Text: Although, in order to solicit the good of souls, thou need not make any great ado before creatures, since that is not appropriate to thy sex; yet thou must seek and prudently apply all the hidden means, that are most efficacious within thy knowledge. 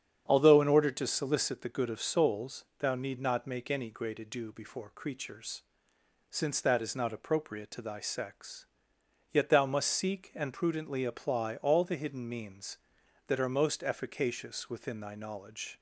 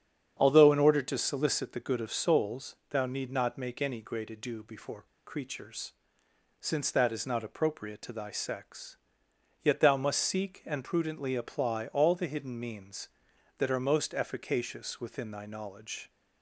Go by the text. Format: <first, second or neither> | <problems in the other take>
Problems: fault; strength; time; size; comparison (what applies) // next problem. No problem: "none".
first | starts louder than the rest; strong; until 1.4 s; 8 dB; strong in the first // pauses between "before" and "creatures"; slight; at 5.0 s; 0.22 s long